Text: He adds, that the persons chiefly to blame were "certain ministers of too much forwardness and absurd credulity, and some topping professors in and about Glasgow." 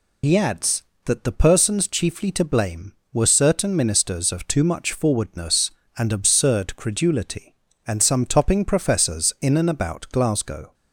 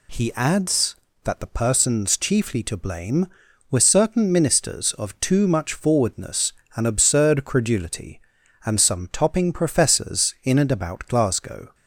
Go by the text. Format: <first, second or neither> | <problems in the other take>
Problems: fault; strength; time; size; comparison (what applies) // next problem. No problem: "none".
second | loses the start of "He"; at 0.2 s; 100 ms